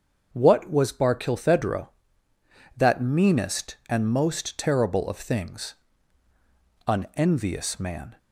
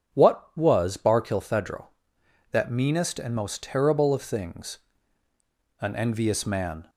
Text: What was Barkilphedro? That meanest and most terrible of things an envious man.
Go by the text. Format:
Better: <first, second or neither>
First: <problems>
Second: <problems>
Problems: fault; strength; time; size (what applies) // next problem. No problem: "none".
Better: neither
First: starts louder than the rest; until 1.3 s; 7 dB // pauses between "things" and "an"; at 5.7 s; 1.1 s long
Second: starts louder than the rest; strong; until 1.2 s; 8 dB // pauses between "things" and "an"; at 4.7 s; 1.0 s long